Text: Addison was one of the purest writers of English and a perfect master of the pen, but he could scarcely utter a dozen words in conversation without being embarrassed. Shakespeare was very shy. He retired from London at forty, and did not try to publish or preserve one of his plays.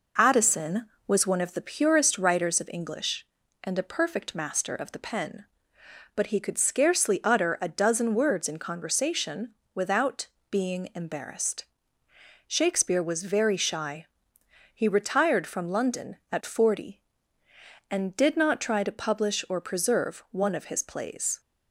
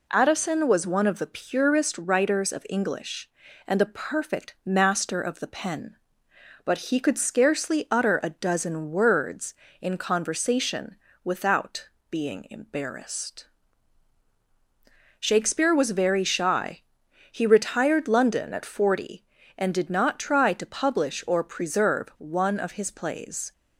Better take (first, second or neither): first